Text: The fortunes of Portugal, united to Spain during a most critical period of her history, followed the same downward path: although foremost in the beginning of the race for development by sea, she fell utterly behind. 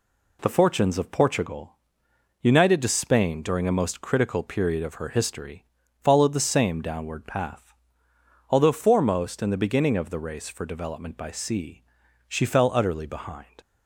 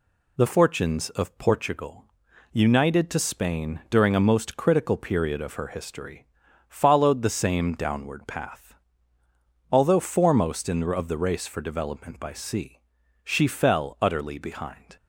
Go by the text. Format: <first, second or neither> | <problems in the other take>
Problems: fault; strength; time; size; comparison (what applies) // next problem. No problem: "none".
first | skips "beginning"; at 10.9 s